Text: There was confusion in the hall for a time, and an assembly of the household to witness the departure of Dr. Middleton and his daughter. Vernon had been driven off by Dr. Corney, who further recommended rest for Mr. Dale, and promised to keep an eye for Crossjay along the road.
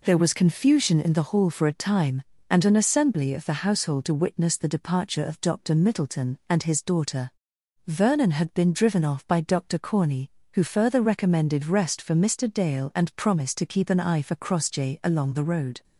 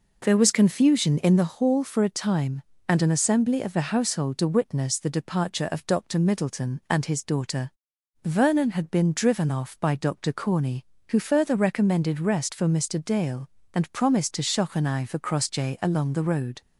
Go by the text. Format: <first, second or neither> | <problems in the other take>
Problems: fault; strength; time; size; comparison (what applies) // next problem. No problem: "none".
first | says "shock" for "keep"; at 14.4 s